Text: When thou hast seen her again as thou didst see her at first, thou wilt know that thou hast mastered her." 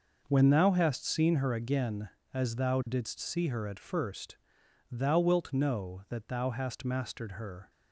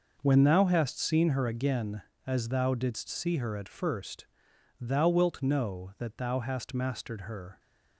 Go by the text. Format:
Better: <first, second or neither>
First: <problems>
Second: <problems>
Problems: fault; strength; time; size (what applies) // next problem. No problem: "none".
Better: neither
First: none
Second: none